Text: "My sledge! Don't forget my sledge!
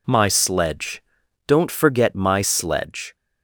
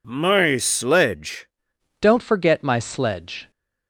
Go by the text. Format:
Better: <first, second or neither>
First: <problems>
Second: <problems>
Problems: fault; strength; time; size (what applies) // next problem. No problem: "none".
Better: first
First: none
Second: changes voice at "Don't"; from 2.0 s on; 1.5 s long